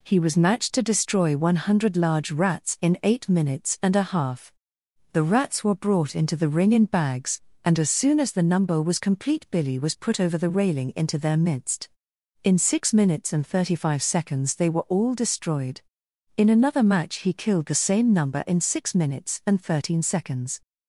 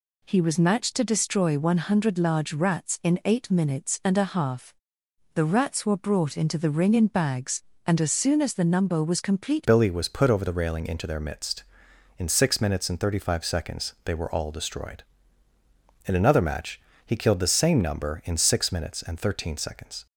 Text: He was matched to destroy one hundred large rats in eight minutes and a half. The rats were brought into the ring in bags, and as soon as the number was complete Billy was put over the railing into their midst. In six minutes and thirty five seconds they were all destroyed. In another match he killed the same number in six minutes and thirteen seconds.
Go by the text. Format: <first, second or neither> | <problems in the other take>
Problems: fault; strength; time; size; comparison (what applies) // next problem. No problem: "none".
first | changes voice at "Billy"; from 9.6 s on; 10.4 s long // pauses between "match" and "he"; slight; at 16.7 s; 0.26 s long